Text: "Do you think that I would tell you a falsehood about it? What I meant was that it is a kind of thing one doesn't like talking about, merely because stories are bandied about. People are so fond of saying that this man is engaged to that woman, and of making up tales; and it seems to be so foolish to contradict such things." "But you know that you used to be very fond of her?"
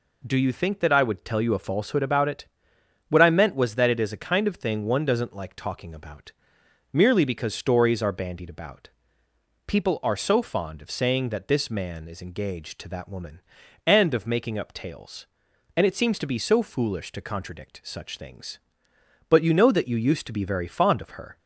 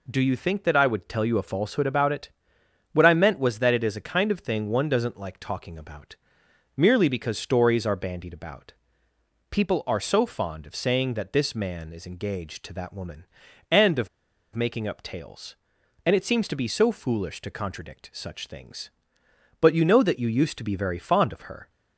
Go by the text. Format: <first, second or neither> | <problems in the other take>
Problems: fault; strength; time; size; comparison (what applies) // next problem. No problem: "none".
first | pauses between "of" and "making"; noticeable; at 14.0 s; 0.46 s long